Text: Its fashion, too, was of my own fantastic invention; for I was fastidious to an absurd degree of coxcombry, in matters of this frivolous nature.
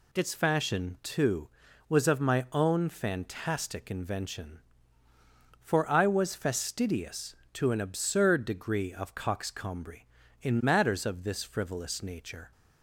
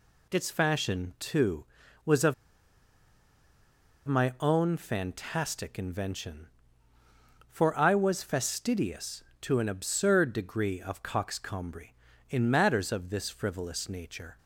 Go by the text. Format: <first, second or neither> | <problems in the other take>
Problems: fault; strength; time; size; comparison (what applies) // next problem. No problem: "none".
first | pauses between "of" and "my"; strong; at 2.3 s; 1.7 s long